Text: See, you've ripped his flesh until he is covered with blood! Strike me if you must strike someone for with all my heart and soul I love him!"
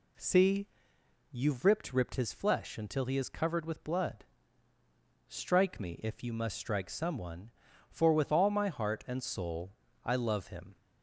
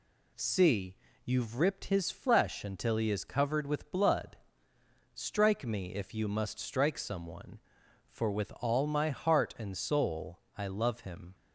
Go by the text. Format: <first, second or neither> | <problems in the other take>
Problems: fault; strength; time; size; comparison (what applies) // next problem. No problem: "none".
second | says "ripped" twice; at 1.9 s // pauses between "soul" and "I"; slight; at 9.7 s; 0.32 s long; slight in the second